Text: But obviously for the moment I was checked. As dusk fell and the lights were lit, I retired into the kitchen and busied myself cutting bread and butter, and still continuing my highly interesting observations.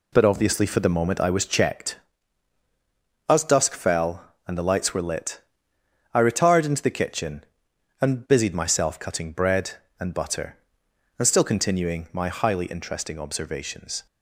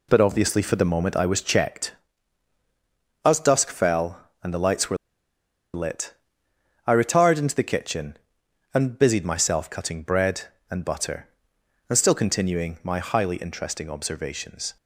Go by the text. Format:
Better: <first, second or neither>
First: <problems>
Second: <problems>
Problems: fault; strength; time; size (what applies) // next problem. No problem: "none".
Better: first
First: none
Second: pauses between "were" and "lit"; noticeable; at 4.9 s; 0.77 s long